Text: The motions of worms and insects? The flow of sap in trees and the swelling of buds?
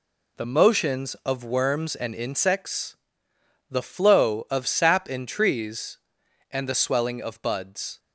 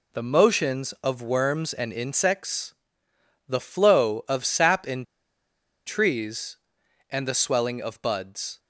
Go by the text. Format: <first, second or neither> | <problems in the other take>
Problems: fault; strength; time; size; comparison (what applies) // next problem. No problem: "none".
first | pauses between "in" and "trees"; noticeable; at 5.0 s; 0.81 s long